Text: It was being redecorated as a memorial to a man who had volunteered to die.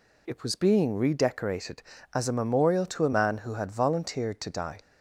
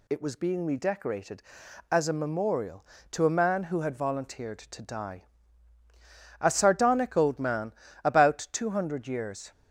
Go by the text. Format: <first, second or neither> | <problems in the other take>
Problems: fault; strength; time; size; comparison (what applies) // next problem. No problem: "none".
first | goes on to say "A sardonic old man about two hundred years"; strong; from 6.3 s on; 3.1 s long